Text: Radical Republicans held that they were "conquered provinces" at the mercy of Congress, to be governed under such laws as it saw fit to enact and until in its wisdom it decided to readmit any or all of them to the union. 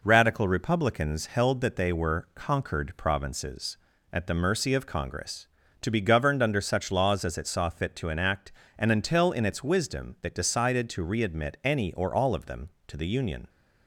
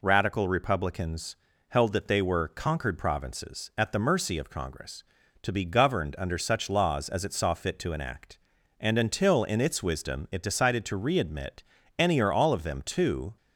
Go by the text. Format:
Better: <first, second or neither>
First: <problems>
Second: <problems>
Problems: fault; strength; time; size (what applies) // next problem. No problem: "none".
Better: first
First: none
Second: pauses between "Republicans" and "held"; slight; at 1.3 s; 0.32 s long // pauses between "readmit" and "any"; slight; at 11.6 s; 0.34 s long // stops before "the union"; at 13.3 s